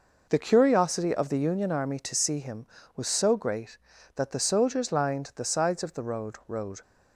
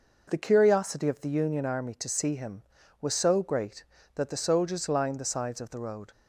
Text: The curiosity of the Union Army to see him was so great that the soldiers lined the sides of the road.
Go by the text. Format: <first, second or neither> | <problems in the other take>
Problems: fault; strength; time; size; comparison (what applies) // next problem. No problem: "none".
second | says "road" twice; at 6.4 s